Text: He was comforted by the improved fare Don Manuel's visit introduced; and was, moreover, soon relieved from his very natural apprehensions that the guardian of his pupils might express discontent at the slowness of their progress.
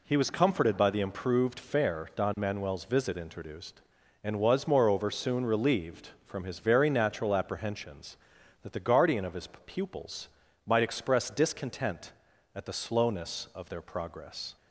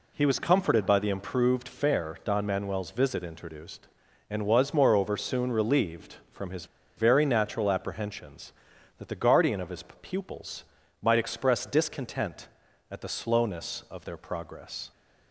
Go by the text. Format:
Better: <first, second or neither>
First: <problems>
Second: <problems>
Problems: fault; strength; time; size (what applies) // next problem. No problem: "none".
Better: first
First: pauses between "his" and "pupils"; slight; at 9.4 s; 0.18 s long // pauses between "pupils" and "might"; slight; at 10.2 s; 0.36 s long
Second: pauses between "his" and "very"; slight; at 6.6 s; 0.30 s long // pauses between "his" and "pupils"; slight; at 9.8 s; 0.18 s long // pauses between "pupils" and "might"; slight; at 10.6 s; 0.36 s long